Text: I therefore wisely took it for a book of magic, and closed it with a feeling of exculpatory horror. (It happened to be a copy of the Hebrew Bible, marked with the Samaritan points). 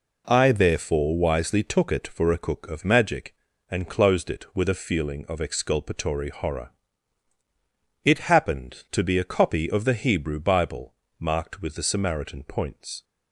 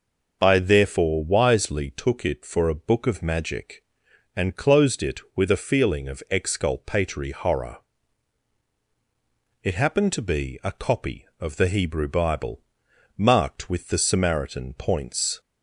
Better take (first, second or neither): second